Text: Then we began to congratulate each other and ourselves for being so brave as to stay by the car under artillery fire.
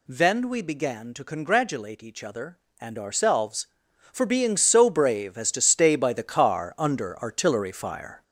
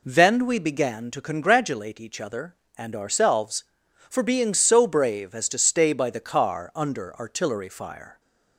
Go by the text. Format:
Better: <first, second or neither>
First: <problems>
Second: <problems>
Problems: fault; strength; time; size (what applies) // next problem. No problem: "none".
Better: second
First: gets louder; noticeable; throughout; 5 dB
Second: none